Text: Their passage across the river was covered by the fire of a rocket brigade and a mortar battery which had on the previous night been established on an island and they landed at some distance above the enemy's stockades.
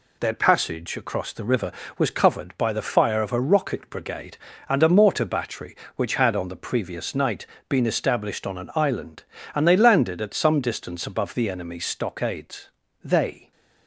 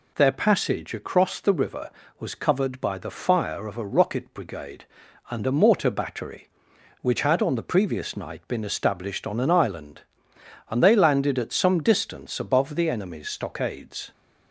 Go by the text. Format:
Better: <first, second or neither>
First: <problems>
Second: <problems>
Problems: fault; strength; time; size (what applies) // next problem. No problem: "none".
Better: second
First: pauses between "night" and "been"; slight; at 7.4 s; 0.24 s long // goes on to say "They"; slight; from 13.0 s on; 0.48 s long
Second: none